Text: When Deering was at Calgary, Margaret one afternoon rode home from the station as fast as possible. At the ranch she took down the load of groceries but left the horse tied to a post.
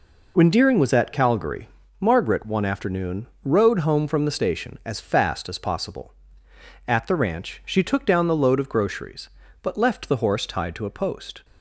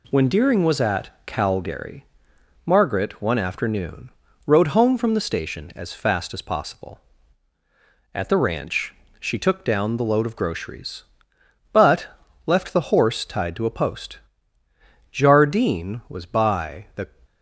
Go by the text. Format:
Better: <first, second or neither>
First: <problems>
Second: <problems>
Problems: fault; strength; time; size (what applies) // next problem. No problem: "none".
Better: first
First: pauses between "afternoon" and "rode"; slight; at 3.2 s; 0.18 s long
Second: pauses between "at" and "Calgary"; slight; at 1.0 s; 0.16 s long // pauses between "afternoon" and "rode"; slight; at 4.1 s; 0.34 s long // pauses between "ranch" and "she"; slight; at 8.9 s; 0.26 s long // pauses between "but" and "left"; at 12.0 s; 0.38 s long // goes on to say "Jardine was by the"; from 15.4 s on; 1.6 s long